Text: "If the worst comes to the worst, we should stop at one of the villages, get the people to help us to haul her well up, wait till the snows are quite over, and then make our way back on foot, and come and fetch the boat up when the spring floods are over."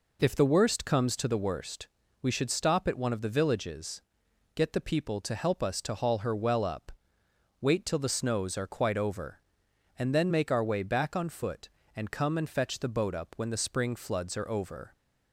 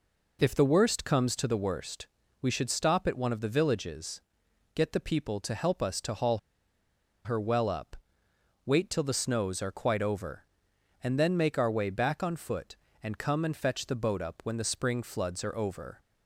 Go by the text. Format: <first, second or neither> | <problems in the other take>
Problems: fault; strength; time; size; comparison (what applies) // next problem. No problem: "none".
first | pauses between "haul" and "her"; noticeable; at 6.3 s; 0.86 s long